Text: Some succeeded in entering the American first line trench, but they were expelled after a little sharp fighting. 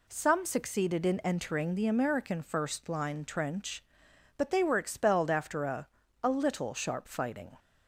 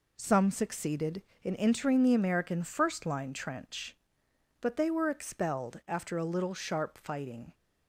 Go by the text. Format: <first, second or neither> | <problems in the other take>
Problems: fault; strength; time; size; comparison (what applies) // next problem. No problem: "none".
second | says "a" twice; at 6.2 s